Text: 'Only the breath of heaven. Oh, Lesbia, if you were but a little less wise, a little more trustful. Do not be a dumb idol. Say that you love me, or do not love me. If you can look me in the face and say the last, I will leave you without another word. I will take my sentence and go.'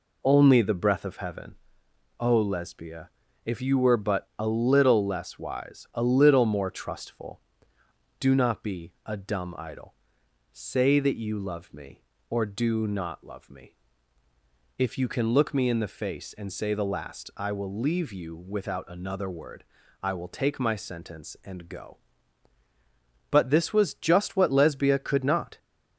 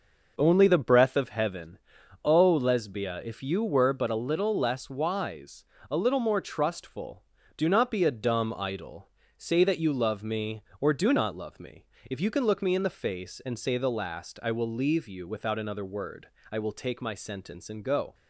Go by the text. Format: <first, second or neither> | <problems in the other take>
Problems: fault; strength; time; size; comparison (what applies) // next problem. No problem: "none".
second | goes on to say "But this was just what Lesbia could not"; strong; from 23.3 s on; 2.2 s long